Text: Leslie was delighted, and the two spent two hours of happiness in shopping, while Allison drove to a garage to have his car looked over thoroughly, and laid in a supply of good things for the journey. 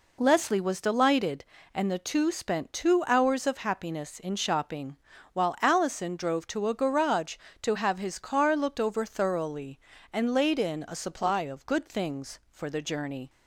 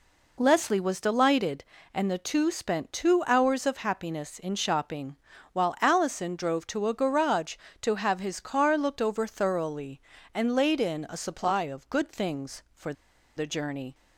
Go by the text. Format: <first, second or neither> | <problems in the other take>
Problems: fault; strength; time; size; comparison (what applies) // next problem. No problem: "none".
first | pauses between "for" and "the"; at 12.9 s; 0.43 s long